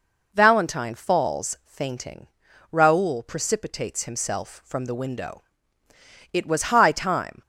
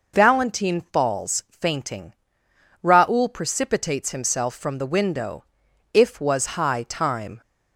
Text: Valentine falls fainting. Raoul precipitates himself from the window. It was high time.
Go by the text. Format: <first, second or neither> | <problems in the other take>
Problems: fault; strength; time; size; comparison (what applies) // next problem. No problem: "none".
first | says "If" for "It"; at 5.9 s